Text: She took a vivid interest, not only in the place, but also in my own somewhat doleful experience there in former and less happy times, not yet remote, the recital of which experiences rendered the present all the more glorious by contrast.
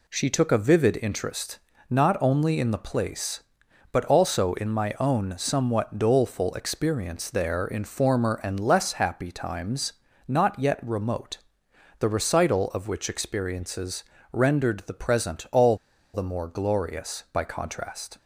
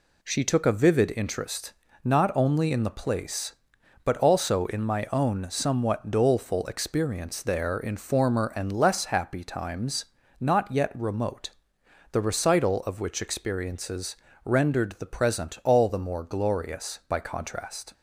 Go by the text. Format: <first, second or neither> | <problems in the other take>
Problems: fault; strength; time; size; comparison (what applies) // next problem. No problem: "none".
second | pauses between "experiences" and "rendered"; slight; at 14.0 s; 0.30 s long; slight in the second // pauses between "all" and "the"; at 15.7 s; 0.36 s long